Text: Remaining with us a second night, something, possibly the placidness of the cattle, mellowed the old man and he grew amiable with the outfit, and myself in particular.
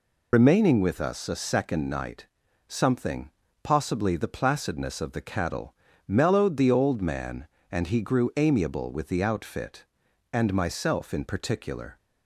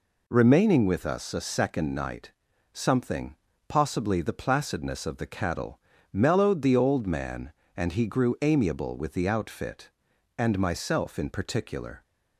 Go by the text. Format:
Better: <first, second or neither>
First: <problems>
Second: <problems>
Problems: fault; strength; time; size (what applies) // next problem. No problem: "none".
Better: second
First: loses the start of "Remaining"; at 0.3 s; 100 ms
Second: none